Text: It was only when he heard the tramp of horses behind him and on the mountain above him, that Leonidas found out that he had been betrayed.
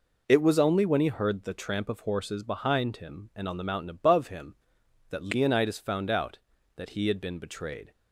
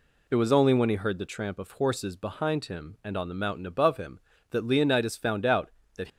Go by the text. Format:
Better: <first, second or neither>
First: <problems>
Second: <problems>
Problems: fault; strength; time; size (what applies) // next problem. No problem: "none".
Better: first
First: none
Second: stops before "he had been betrayed"; at 6.0 s